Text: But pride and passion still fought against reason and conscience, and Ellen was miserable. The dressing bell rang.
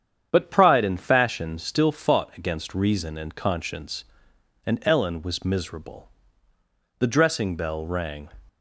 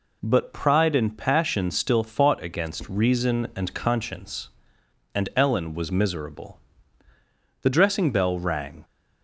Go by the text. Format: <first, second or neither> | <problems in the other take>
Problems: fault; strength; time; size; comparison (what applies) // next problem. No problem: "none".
second | starts louder than the rest; strong; until 1.3 s; 8.5 dB // says "fashion" for "passion"; at 0.9 s